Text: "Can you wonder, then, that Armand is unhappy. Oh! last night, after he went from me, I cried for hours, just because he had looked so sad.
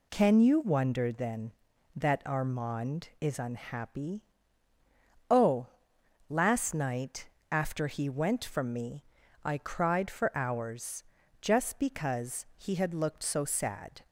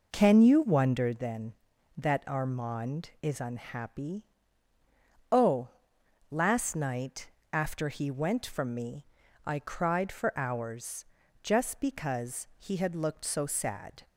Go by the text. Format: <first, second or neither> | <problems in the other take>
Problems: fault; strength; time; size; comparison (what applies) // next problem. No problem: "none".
first | starts louder than the rest; noticeable; until 1.2 s; 5 dB